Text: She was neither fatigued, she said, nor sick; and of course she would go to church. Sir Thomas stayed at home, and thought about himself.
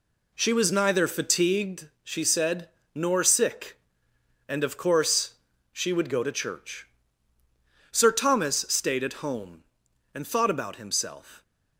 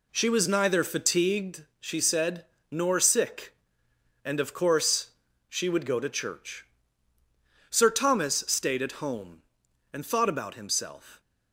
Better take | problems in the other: neither | pauses between "course" and "she"; the same in both

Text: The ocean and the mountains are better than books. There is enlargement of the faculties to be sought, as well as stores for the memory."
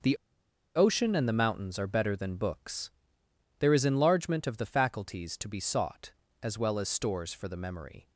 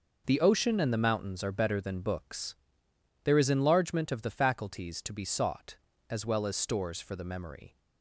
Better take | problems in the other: second | pauses between "The" and "ocean"; noticeable; at 0.1 s; 0.59 s long

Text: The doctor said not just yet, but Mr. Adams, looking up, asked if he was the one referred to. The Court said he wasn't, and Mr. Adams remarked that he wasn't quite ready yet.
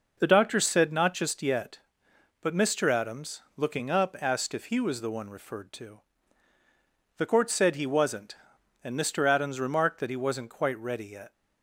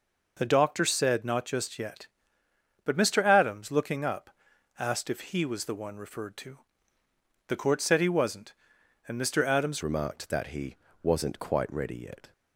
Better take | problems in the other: first | changes voice at "remarked"; from 9.8 s on; 2.5 s long // pauses between "he" and "wasn't"; slight; at 10.7 s; 0.26 s long

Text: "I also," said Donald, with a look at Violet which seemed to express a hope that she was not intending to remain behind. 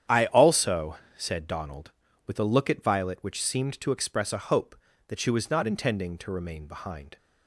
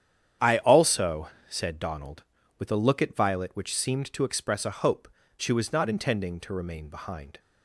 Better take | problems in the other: first | starts louder than the rest; strong; until 1.6 s; 9 dB; strong in the first // skips "that"; at 5.2 s

